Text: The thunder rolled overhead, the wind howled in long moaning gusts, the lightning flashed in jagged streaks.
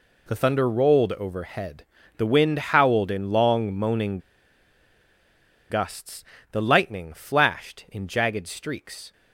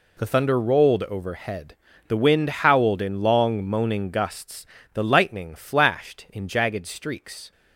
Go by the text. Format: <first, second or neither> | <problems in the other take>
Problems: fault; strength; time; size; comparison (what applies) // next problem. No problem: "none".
second | pauses between "moaning" and "gusts"; strong; at 4.1 s; 1.5 s long